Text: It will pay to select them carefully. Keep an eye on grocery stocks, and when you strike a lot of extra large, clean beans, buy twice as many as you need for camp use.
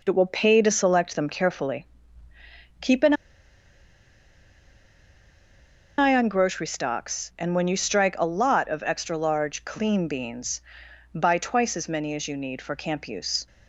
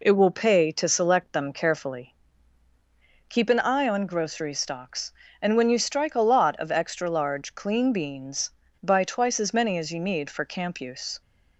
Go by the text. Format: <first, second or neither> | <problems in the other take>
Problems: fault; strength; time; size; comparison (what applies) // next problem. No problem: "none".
second | pauses between "an" and "eye"; strong; at 3.1 s; 2.8 s long